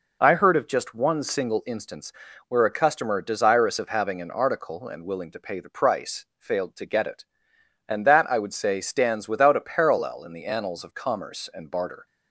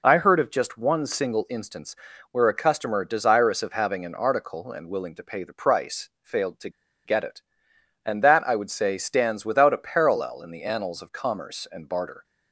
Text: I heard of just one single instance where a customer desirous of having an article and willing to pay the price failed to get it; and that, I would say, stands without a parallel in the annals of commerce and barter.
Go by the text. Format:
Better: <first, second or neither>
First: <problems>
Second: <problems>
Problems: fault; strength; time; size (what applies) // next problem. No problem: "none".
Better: first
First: pauses between "instance" and "where"; slight; at 2.1 s; 0.34 s long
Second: pauses between "instance" and "where"; slight; at 1.9 s; 0.34 s long // pauses between "to" and "get"; slight; at 6.6 s; 0.35 s long